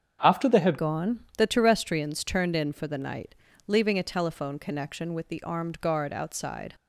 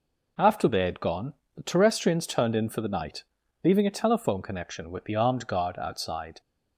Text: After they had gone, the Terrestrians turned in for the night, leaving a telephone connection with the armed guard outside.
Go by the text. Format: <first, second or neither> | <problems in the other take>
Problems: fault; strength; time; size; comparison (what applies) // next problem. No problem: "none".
second | starts louder than the rest; strong; until 1.4 s; 7.5 dB // changes voice at "gone"; from 0.7 s on; 6.0 s long